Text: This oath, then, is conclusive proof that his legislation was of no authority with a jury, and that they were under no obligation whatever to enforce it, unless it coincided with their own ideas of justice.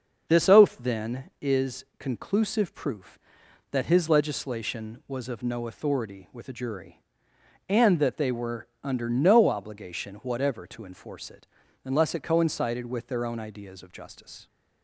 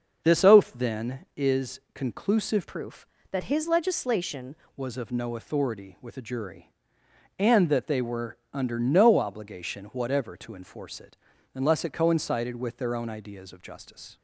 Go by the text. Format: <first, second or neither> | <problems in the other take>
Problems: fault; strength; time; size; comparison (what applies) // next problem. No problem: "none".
first | starts louder than the rest; until 1.3 s; 6.5 dB // changes voice from "proof" to "legislation"; from 2.6 to 4.5 s; 1.9 s long // pauses between "were" and "under"; slight; at 8.3 s; 0.16 s long; slight in the first